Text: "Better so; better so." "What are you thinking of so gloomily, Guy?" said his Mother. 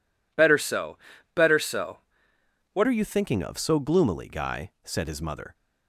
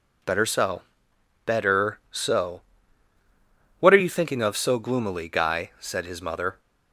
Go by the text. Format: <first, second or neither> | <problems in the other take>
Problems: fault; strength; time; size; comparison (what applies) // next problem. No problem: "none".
second | changes voice at "are"; from 2.8 s on; 2.7 s long